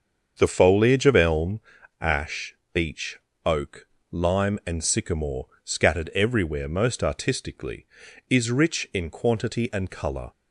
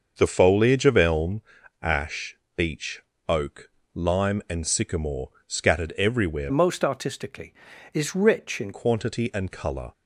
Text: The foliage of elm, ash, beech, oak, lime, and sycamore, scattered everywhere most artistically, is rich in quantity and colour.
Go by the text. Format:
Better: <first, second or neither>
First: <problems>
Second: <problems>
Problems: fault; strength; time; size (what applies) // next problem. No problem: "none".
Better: first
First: starts louder than the rest; until 1.3 s; 7 dB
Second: starts louder than the rest; until 1.1 s; 6.5 dB // changes voice from "most" to "in"; from 6.4 to 8.7 s; 2.3 s long